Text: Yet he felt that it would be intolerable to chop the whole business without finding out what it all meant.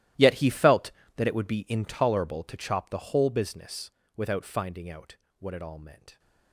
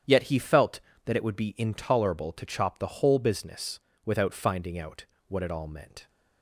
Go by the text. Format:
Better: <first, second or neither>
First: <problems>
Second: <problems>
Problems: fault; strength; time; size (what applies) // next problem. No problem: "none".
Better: second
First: gets quieter; strong; throughout; 18.5 dB // starts louder than the rest; strong; until 1.4 s; 14 dB // pauses between "business" and "without"; slight; at 3.9 s; 0.26 s long // pauses between "out" and "what"; slight; at 5.1 s; 0.22 s long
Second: starts louder than the rest; strong; until 1.3 s; 9 dB // pauses between "business" and "without"; slight; at 3.7 s; 0.26 s long // pauses between "out" and "what"; slight; at 5.0 s; 0.22 s long